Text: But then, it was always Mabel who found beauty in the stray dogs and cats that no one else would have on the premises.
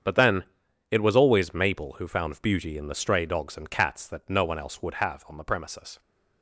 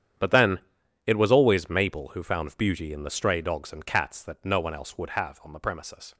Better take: first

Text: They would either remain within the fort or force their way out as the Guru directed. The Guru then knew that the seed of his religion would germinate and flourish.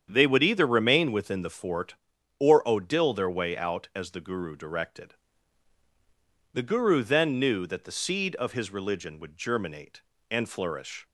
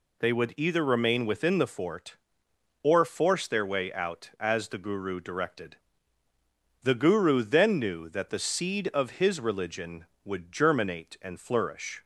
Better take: second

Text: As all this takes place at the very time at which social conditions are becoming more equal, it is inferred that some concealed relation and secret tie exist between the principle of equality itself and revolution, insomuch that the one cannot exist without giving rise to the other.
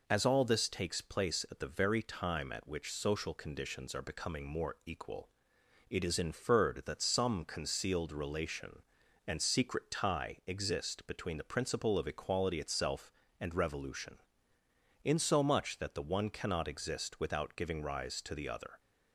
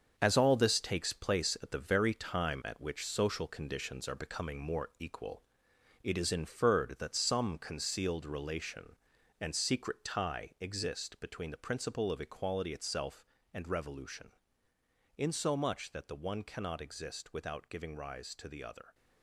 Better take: first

